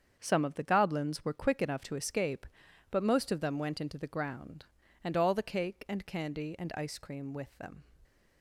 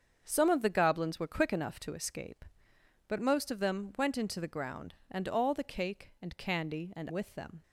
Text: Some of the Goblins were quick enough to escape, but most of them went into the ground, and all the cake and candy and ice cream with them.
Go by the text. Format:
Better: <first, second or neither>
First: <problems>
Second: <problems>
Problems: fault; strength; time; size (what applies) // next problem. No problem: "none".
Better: first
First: starts louder than the rest; strong; until 1.2 s; 7.5 dB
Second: starts louder than the rest; strong; until 1.2 s; 7 dB // skips "ice cream"; at 7.0 s